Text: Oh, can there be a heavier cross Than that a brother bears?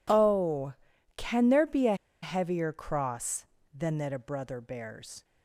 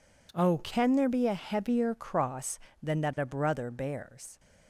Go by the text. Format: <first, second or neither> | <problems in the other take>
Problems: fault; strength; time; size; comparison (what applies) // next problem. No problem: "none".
second | pauses between "a" and "heavier"; slight; at 1.9 s; 0.27 s long